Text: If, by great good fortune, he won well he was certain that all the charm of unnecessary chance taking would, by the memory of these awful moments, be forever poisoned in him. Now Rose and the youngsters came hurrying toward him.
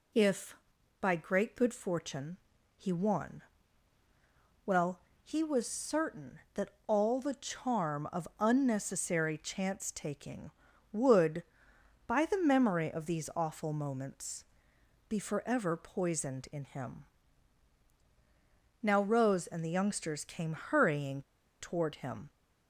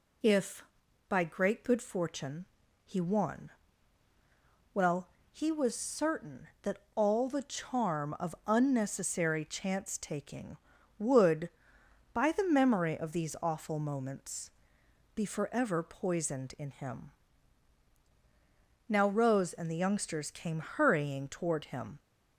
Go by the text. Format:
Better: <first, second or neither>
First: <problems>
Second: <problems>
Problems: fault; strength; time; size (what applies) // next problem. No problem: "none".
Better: second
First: pauses between "won" and "well"; at 3.4 s; 1.2 s long // pauses between "well" and "he"; slight; at 5.0 s; 0.22 s long // pauses between "that" and "all"; slight; at 6.6 s; 0.18 s long // pauses between "hurrying" and "toward"; at 21.2 s; 0.37 s long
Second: pauses between "won" and "well"; at 3.5 s; 1.2 s long // pauses between "well" and "he"; slight; at 5.0 s; 0.22 s long // pauses between "that" and "all"; slight; at 6.7 s; 0.18 s long